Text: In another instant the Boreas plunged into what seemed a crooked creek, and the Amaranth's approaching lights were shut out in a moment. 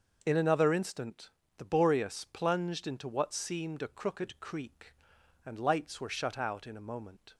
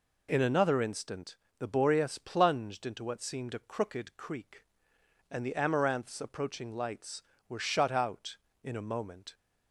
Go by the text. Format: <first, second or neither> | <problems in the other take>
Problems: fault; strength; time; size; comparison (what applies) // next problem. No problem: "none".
second | starts louder than the rest; until 1.2 s; 6.5 dB // pauses between "instant" and "the"; slight; at 1.3 s; 0.26 s long; slight in the second // skips "the Amaranth's approaching"; at 5.5 s